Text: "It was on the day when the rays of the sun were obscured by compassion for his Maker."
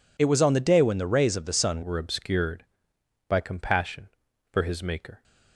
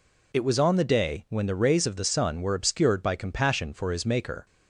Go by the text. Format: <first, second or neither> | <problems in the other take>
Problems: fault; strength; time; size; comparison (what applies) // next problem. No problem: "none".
second | changes voice at "were"; from 1.8 s on; 3.4 s long